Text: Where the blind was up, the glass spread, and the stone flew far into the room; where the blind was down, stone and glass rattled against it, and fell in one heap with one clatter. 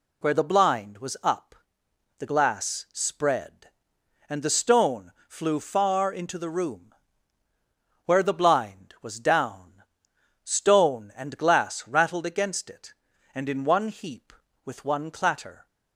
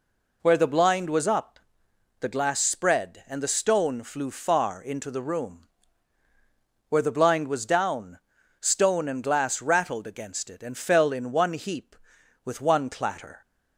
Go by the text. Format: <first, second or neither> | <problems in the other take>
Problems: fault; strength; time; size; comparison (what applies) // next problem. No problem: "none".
second | pauses between "stone" and "flew"; slight; at 5.1 s; 0.18 s long // skips "fell"; at 13.4 s